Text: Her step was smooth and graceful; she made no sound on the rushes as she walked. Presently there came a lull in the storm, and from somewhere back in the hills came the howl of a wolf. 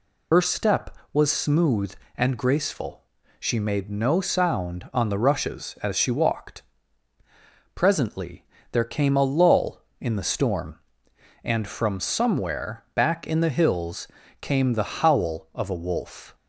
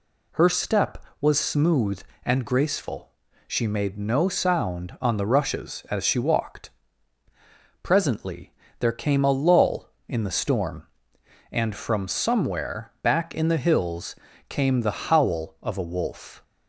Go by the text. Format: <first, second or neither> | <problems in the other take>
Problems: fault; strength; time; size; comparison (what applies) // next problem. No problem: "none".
second | loses the start of "Her"; at 0.3 s; 75 ms // pauses between "Presently" and "there"; slight; at 8.4 s; 0.26 s long; slight in the second // pauses between "hills" and "came"; slight; at 14.0 s; 0.34 s long; slight in the second